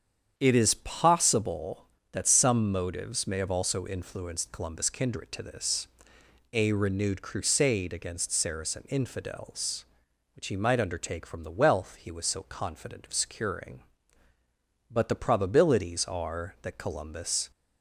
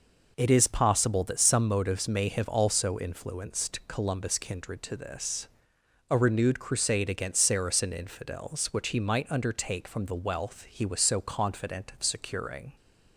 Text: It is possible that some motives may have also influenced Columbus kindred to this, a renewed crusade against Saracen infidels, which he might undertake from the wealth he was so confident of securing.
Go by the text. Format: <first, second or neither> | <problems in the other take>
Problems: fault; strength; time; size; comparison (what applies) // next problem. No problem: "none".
second | starts louder than the rest; strong; until 1.3 s; 8 dB // goes on to say "But the probabilities are that Columbus"; strong; from 14.9 s on; 2.6 s long